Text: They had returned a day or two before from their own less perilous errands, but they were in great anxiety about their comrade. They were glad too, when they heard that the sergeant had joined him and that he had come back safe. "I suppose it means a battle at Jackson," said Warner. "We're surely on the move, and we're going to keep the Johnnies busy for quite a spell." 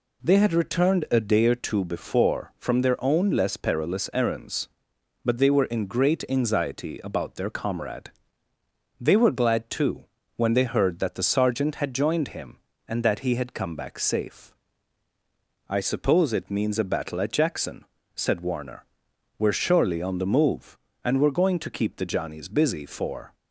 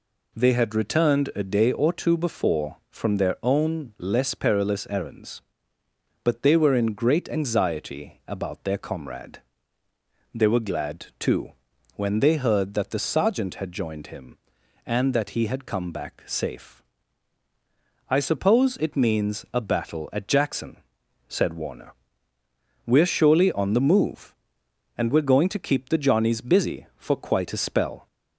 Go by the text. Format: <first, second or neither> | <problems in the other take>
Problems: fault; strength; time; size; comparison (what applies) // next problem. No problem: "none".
second | stops before "quite a spell"; at 23.3 s